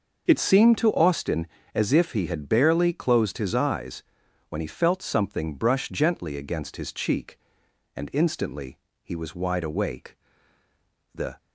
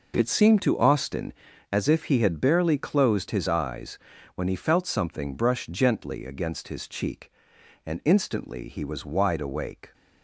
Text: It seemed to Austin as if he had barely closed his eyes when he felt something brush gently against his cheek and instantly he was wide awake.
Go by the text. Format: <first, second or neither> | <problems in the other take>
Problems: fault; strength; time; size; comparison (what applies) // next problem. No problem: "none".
second | pauses between "eyes" and "when"; noticeable; at 4.0 s; 0.46 s long; also in the second // pauses between "instantly" and "he"; slight; at 8.7 s; 0.26 s long // goes on to say "The"; slight; from 11.1 s on; 0.24 s long